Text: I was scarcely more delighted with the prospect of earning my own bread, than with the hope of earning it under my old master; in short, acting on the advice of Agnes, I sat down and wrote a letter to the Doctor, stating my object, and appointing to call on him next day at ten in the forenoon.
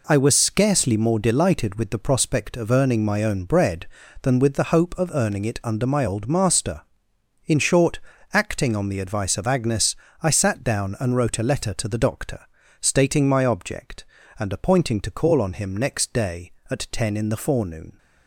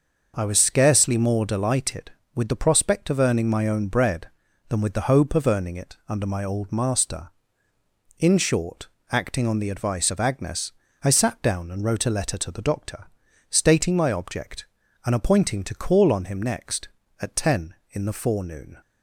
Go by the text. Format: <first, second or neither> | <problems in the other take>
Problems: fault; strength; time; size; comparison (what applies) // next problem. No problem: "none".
first | skips "day"; at 17.0 s